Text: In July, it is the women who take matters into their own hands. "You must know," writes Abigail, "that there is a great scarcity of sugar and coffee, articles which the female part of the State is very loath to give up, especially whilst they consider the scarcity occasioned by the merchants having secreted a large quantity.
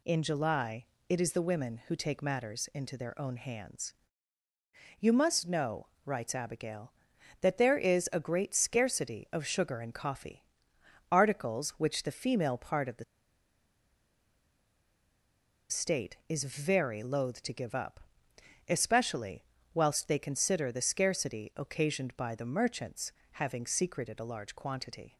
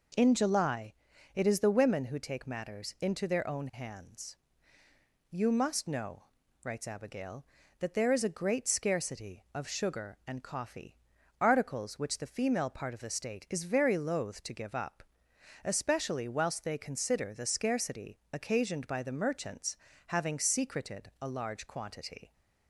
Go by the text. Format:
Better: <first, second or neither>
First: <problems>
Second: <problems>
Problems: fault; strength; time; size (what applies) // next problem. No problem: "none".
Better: second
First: pauses between "the" and "State"; strong; at 13.0 s; 2.6 s long // pauses between "especially" and "whilst"; slight; at 19.4 s; 0.28 s long // pauses between "merchants" and "having"; slight; at 23.1 s; 0.20 s long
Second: pauses between "merchants" and "having"; slight; at 19.7 s; 0.30 s long